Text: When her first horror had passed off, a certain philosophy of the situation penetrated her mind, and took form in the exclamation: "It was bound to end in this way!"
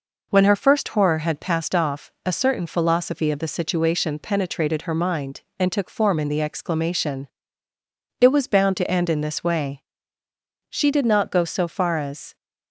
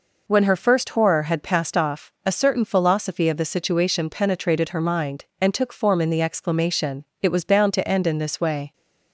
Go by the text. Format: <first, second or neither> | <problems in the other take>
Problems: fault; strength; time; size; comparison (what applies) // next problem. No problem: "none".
second | goes on to say "She did not go so far as"; from 10.6 s on; 1.6 s long